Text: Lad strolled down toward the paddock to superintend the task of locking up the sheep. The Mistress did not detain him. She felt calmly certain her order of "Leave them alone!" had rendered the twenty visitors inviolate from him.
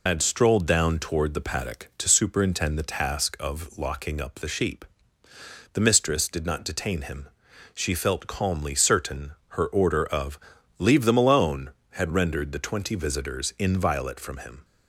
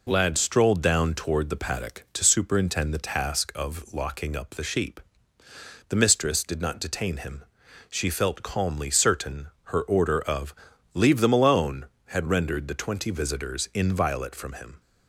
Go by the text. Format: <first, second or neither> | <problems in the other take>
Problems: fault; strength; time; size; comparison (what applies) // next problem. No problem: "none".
second | loses the start of "Lad"; at 0.0 s; 140 ms // pauses between "certain" and "her"; slight; at 9.3 s; 0.16 s long; slight in the second // pauses between "of" and "Leave"; at 10.3 s; 0.40 s long; also in the second